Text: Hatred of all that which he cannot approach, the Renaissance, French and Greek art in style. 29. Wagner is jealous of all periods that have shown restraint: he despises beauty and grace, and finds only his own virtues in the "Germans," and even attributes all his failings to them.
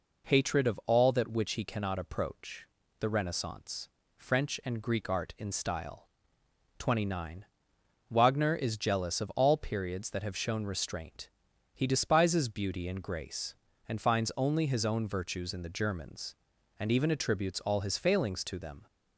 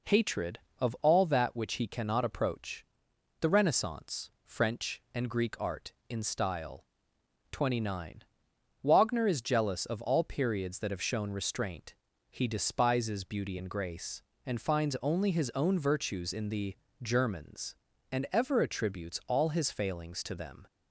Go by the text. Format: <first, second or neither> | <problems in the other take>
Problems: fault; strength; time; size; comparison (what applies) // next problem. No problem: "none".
first | pauses between "the" and "Germans"; slight; at 16.7 s; 0.26 s long // says "ever" for "even"; at 18.3 s